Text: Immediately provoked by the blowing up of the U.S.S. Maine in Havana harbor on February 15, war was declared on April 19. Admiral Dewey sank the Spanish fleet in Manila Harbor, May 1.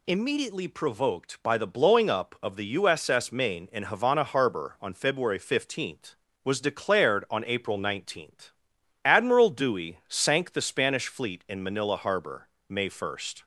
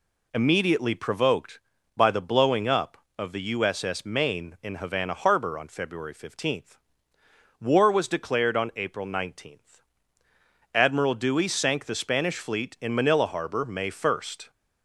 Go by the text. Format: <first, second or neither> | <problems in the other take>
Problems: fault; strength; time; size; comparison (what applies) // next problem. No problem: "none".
second | skips "war"; at 6.2 s